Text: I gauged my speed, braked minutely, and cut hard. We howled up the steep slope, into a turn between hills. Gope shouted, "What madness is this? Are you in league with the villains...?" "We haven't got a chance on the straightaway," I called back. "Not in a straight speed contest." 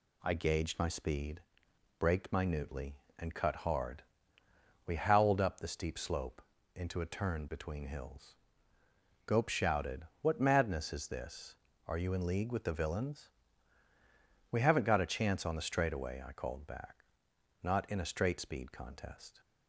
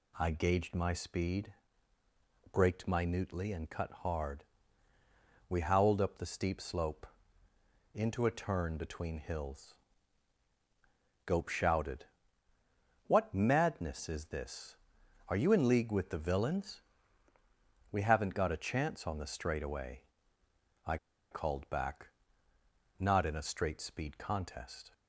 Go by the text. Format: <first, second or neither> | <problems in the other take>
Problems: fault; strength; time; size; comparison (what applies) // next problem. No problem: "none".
first | pauses between "I" and "called"; slight; at 20.9 s; 0.34 s long